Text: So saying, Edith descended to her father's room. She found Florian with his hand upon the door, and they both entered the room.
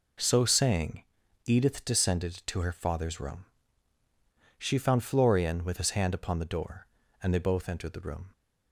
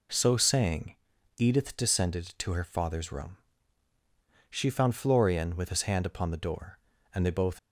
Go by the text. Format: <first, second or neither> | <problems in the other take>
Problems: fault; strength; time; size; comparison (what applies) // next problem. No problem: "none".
first | stops before "entered the room"; at 7.5 s